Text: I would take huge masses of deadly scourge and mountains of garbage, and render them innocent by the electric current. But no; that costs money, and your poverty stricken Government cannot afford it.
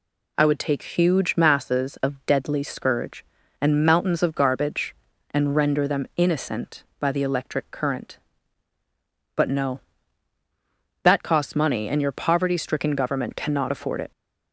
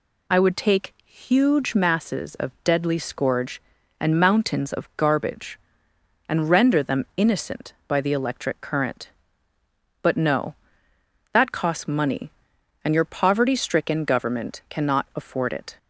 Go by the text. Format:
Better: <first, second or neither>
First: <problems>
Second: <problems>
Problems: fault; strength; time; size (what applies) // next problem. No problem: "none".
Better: neither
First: none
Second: none